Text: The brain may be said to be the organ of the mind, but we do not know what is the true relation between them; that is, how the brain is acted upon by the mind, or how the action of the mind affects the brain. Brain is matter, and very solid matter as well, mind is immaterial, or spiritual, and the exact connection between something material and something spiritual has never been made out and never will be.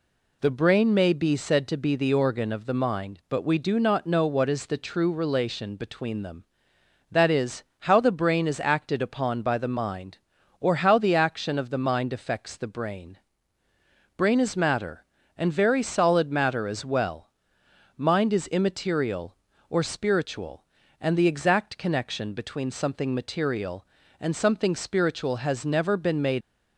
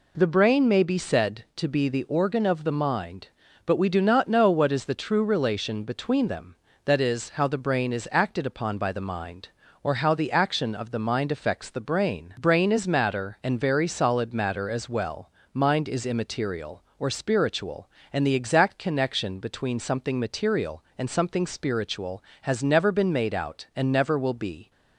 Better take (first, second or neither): second